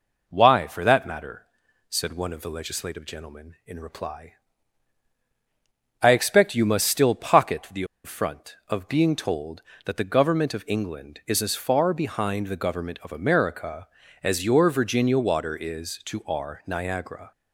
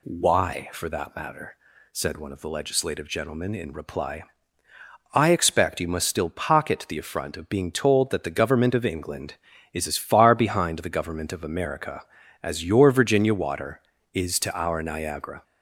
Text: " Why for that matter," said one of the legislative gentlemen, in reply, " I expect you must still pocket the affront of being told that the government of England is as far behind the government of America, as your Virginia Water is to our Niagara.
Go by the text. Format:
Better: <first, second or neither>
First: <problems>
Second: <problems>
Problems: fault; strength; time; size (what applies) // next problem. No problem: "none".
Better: second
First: pauses between "the" and "affront"; slight; at 7.8 s; 0.20 s long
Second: none